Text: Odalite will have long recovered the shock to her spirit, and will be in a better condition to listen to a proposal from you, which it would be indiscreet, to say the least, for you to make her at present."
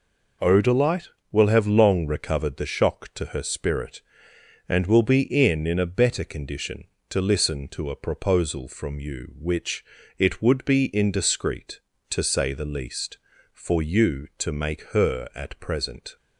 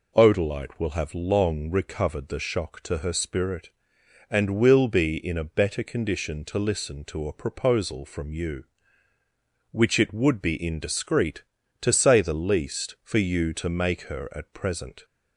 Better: second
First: says "in" twice; at 5.6 s // pauses between "which" and "it"; slight; at 9.8 s; 0.34 s long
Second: none

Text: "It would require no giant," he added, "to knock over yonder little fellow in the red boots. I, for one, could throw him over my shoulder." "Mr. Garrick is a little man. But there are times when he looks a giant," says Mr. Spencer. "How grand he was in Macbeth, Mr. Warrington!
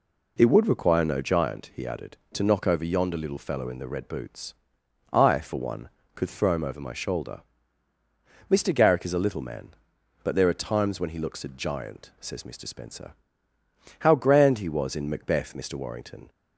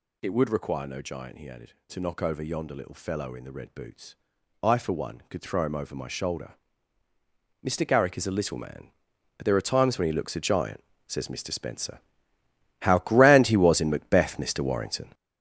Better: first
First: none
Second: gets louder; strong; throughout; 8 dB

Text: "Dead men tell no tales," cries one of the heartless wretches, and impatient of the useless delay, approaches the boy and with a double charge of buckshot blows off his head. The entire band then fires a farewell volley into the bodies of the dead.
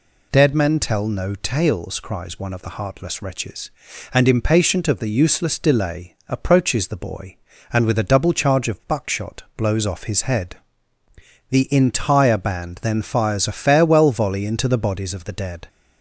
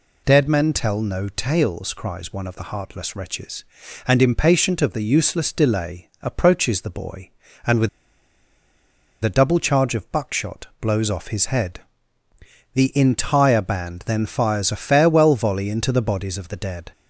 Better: first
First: none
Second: pauses between "with" and "a"; strong; at 7.8 s; 1.3 s long

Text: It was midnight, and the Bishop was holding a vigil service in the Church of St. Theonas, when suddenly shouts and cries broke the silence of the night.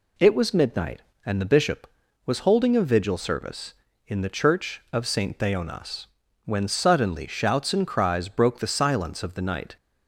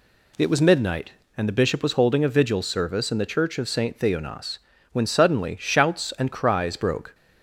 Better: first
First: none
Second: stops before "the silence of the night"; at 7.1 s

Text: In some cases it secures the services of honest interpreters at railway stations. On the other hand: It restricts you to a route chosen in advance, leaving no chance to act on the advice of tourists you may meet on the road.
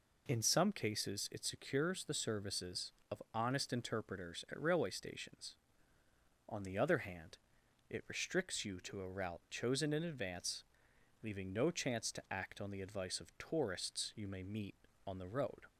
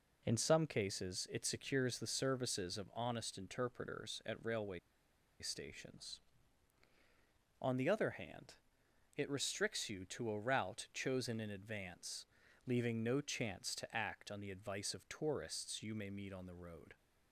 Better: first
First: none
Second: pauses between "railway" and "stations"; noticeable; at 4.7 s; 0.62 s long

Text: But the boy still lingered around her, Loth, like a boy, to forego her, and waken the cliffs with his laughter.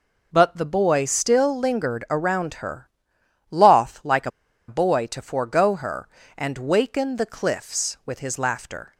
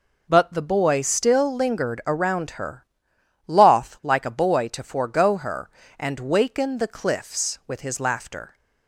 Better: second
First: pauses between "a" and "boy"; at 4.3 s; 0.38 s long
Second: none

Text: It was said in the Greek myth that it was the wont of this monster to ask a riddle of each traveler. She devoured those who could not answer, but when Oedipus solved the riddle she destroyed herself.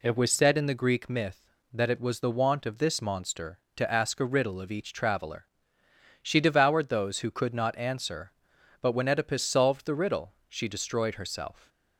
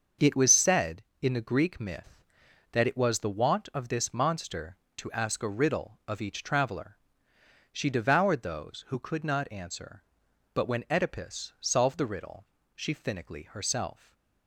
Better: first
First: pauses between "riddle" and "she"; slight; at 10.3 s; 0.16 s long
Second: starts louder than the rest; until 1.4 s; 6.5 dB // pauses between "riddle" and "she"; slight; at 12.4 s; 0.30 s long // says "finically" for "destroyed"; at 12.9 s // stays silent after the last word; slight; from 13.9 s on; 0.5 s long

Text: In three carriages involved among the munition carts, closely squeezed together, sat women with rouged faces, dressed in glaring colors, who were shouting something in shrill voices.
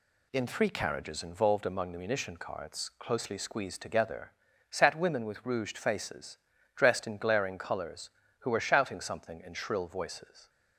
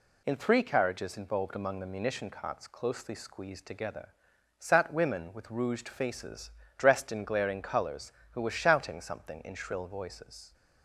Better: neither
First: none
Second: none

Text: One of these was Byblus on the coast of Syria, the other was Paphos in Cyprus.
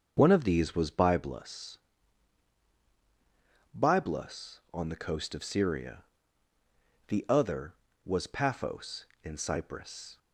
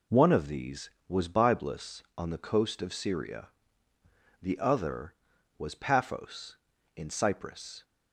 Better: second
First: starts louder than the rest; strong; until 1.1 s; 7 dB // says "Byblus" twice; at 3.7 s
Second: none

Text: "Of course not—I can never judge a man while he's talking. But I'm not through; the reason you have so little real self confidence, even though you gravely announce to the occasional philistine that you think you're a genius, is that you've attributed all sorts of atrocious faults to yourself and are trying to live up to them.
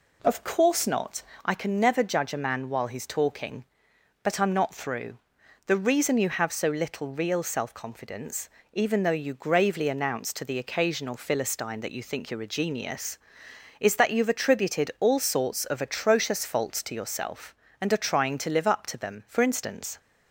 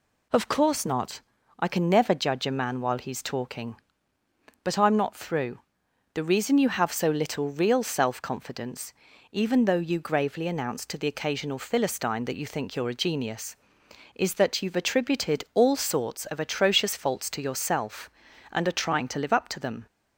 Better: second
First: goes on to say "For instance"; noticeable; from 19.2 s on; 0.70 s long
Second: none

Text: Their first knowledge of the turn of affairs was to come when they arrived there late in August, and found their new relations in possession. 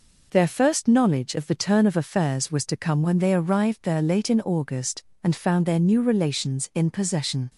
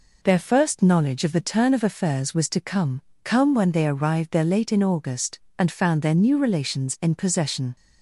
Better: first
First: none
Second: says "come" twice; at 3.2 s

